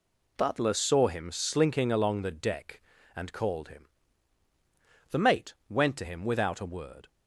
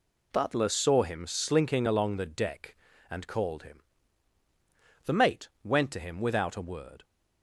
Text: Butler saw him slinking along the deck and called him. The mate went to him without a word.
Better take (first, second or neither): neither